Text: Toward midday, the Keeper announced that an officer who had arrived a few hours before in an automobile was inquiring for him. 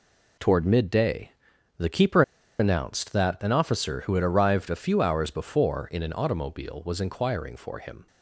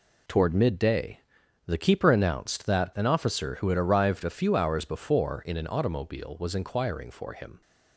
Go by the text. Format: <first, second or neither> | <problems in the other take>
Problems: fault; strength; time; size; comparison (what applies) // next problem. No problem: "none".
second | pauses between "Keeper" and "announced"; at 2.2 s; 0.37 s long